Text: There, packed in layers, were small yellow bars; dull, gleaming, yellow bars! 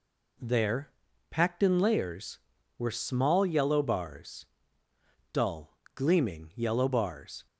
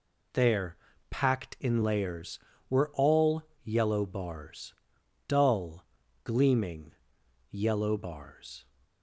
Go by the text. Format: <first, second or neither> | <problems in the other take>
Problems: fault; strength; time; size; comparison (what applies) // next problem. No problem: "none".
first | says "all" for "small"; at 2.9 s